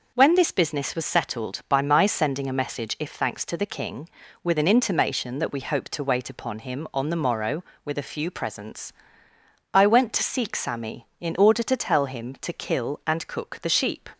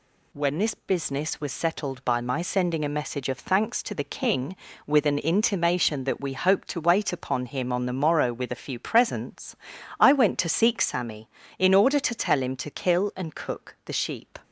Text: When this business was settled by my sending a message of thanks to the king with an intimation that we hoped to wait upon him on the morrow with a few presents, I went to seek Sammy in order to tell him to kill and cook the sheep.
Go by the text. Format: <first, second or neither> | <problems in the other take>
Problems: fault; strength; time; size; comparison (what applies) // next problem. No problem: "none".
second | starts louder than the rest; until 1.1 s; 6 dB // says "if" for "of"; at 2.9 s